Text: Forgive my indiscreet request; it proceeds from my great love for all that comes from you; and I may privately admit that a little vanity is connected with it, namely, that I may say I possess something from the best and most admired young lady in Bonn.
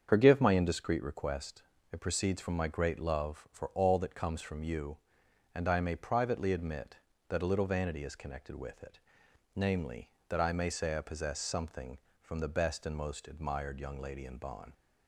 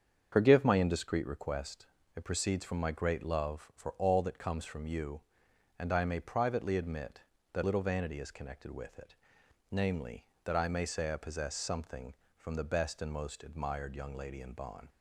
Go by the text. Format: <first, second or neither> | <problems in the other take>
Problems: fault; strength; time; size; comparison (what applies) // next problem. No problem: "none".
first | starts louder than the rest; strong; until 1.3 s; 7.5 dB; strong in the first // skips "a"; at 7.6 s